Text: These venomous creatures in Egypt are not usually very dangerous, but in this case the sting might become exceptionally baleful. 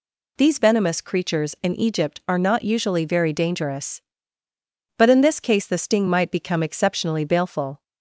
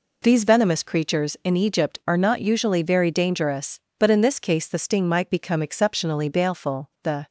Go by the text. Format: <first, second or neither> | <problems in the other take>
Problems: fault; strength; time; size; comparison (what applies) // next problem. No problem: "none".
first | goes on to say "The"; slight; from 7.0 s on; 0.24 s long